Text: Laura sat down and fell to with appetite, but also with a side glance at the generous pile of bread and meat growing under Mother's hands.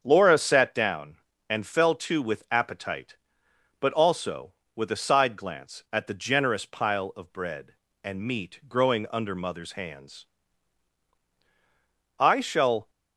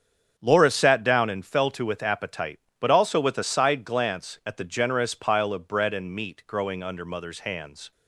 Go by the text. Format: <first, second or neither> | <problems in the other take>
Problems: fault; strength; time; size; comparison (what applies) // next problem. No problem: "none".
second | starts louder than the rest; strong; until 1.0 s; 7.5 dB; strong in the second // goes on to say "I shall"; noticeable; from 12.1 s on; 0.70 s long